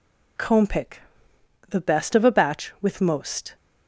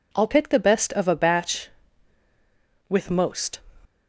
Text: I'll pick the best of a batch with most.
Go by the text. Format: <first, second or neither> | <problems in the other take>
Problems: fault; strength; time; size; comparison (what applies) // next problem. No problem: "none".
second | says "Comb" for "I'll"; at 0.3 s // pauses between "pick" and "the"; noticeable; at 1.0 s; 0.70 s long